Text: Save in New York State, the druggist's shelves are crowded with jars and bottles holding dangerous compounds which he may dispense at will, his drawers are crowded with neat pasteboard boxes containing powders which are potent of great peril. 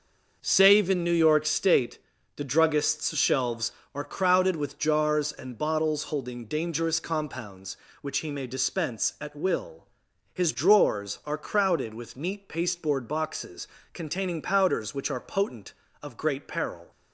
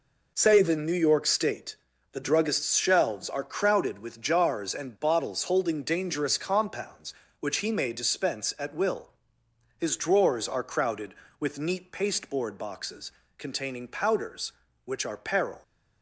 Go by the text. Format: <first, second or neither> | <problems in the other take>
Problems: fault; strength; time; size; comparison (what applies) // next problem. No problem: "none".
first | pauses between "boxes" and "containing"; slight; at 13.1 s; 0.26 s long; slight in the first // skips "potent of great"; at 15.1 s